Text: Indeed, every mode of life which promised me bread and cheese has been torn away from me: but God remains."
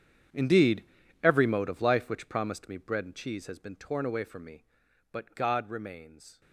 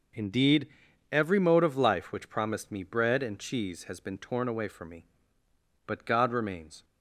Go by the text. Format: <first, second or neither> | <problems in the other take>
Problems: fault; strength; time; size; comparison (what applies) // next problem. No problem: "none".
second | gets quieter; strong; throughout; 17 dB